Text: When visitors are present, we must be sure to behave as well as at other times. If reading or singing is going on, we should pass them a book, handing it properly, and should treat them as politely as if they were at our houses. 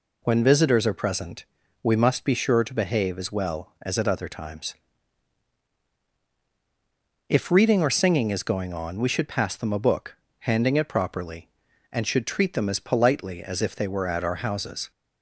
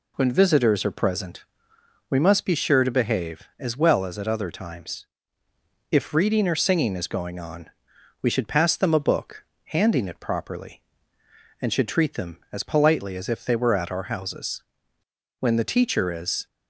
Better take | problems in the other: first | goes on to say "When the teacher is"; noticeable; from 15.3 s on; 1.0 s long

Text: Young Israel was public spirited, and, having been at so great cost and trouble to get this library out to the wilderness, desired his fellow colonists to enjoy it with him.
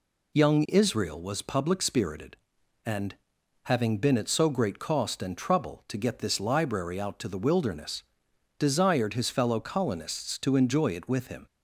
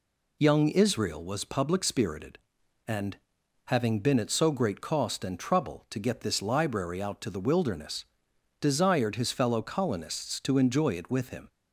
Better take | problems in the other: neither | none

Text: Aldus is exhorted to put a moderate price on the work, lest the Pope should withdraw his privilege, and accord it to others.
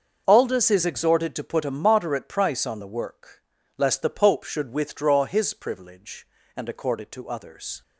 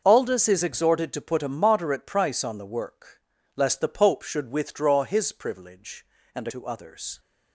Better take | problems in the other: first | starts louder than the rest; until 1.0 s; 6 dB; also in the first // skips "accord it"; at 6.4 s

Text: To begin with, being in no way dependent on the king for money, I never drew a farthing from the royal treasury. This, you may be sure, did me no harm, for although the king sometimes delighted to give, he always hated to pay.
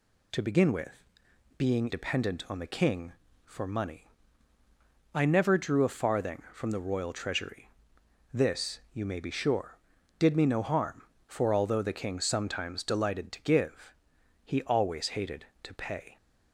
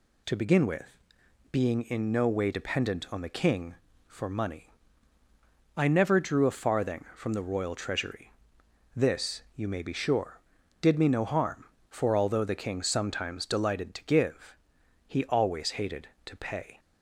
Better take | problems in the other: second | skips "in no way"; at 1.8 s

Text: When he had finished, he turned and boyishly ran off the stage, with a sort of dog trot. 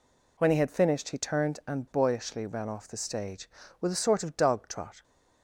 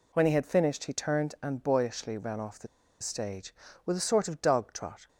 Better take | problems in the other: first | pauses between "the" and "stage"; slight; at 2.6 s; 0.34 s long

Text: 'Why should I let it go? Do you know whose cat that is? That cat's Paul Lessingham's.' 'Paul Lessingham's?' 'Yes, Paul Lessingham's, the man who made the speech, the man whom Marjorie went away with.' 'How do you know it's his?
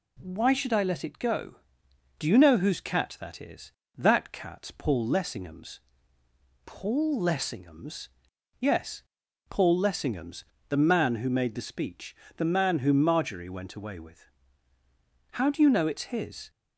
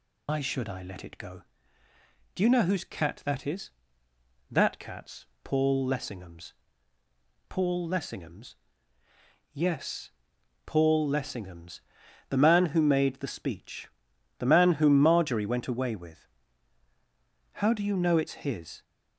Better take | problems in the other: first | loses the start of "Why"; at 0.2 s; 100 ms // pauses between "cat's" and "Paul"; slight; at 5.2 s; 0.16 s long

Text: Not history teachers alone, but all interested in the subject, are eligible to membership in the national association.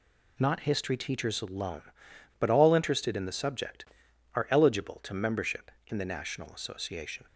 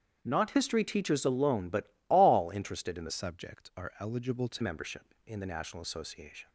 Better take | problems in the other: first | starts louder than the rest; strong; until 1.2 s; 9.5 dB // pauses between "but" and "all"; slight; at 1.9 s; 0.16 s long // changes voice from "subject" to "to"; from 3.0 to 4.6 s; 1.6 s long

